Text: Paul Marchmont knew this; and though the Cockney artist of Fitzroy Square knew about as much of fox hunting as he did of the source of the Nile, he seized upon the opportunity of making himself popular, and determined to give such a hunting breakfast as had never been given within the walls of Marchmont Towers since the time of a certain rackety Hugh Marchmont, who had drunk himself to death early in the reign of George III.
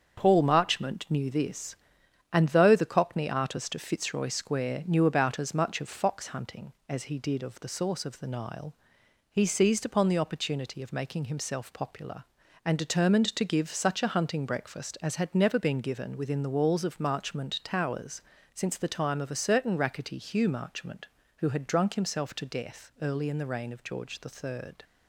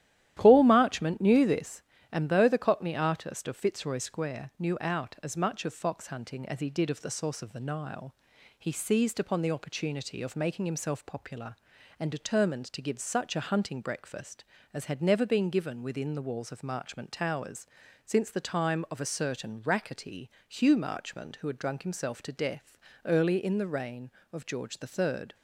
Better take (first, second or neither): first